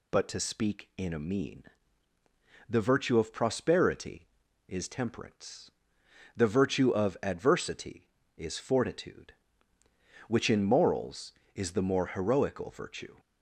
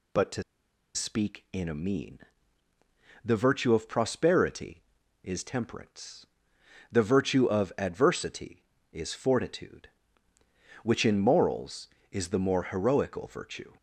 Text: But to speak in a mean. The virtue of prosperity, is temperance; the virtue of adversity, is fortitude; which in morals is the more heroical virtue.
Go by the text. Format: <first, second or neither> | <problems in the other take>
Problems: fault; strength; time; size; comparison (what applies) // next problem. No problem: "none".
first | pauses between "to" and "speak"; noticeable; at 0.4 s; 0.52 s long